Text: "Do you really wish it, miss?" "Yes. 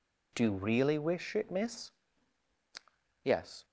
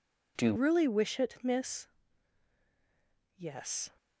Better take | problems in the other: first | changes voice at "really"; from 0.5 s on; 3.4 s long

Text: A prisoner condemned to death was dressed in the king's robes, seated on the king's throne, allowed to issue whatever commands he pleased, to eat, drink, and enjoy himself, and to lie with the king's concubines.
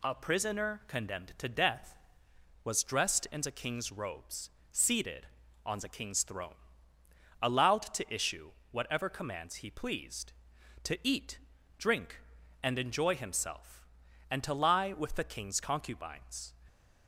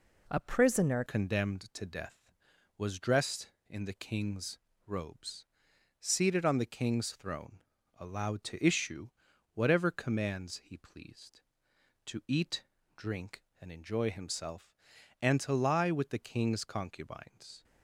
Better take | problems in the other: first | changes voice at "condemned"; from 1.0 s on; 16.6 s long // pauses between "king's" and "robes"; slight; at 4.5 s; 0.30 s long // pauses between "issue" and "whatever"; at 9.0 s; 0.44 s long; slight in the first

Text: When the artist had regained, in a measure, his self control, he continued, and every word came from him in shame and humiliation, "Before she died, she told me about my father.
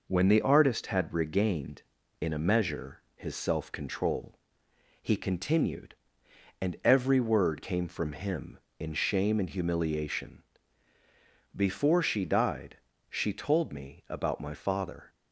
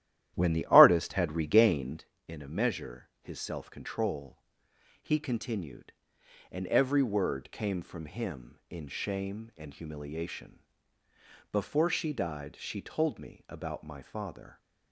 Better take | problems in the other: first | starts louder than the rest; strong; until 2.1 s; 12.5 dB

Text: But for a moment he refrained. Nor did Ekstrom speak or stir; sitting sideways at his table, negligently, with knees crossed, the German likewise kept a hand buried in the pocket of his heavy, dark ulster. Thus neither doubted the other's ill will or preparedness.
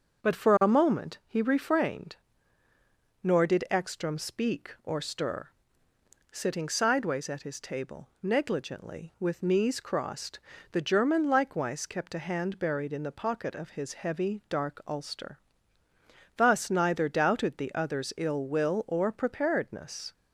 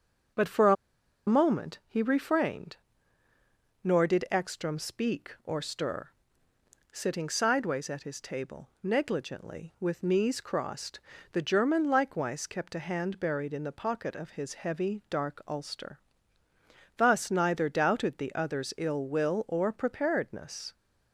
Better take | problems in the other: first | starts louder than the rest; until 1.9 s; 7 dB; also in the first // pauses between "a" and "moment"; noticeable; at 0.7 s; 0.53 s long

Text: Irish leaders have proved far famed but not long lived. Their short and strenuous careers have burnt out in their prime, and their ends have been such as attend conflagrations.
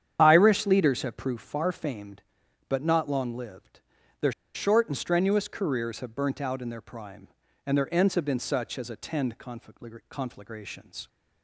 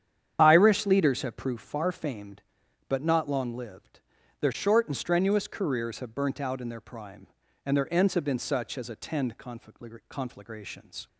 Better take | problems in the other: second | starts louder than the rest; strong; until 1.2 s; 9 dB; strong in the second // pauses between "Their" and "short"; slight; at 4.3 s; 0.23 s long

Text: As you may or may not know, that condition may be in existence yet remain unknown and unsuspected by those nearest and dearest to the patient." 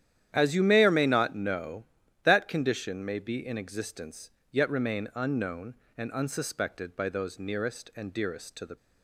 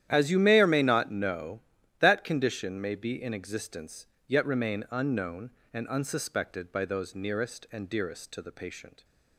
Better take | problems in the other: second | starts louder than the rest; strong; until 1.3 s; 10.5 dB; strong in the second // pauses between "existence" and "yet"; slight; at 4.2 s; 0.22 s long; slight in the second // stops before "patient"; at 8.7 s

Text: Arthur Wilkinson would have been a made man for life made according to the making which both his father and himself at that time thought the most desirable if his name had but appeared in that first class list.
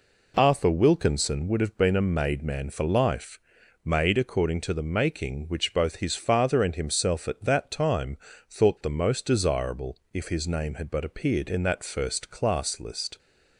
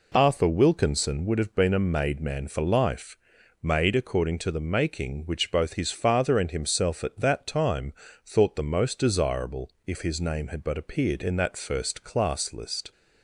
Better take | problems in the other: neither | pauses between "life" and "made"; noticeable; the same in both // pauses between "time" and "thought"; slight; the same in both // pauses between "desirable" and "if"; slight; the same in both

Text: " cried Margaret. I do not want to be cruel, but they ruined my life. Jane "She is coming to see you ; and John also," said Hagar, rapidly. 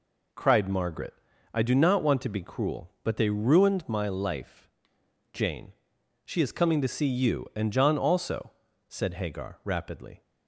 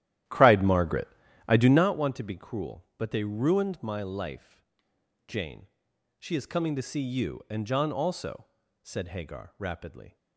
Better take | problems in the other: first | starts louder than the rest; strong; until 1.9 s; 12.5 dB // pauses between "Jane" and "She"; noticeable; at 5.6 s; 0.50 s long; noticeable in the first

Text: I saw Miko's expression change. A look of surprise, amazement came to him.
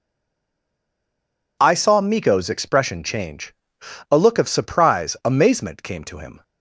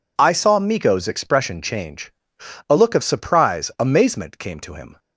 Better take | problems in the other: second | stays silent before the first word; noticeable; until 1.5 s; 1.5 s long

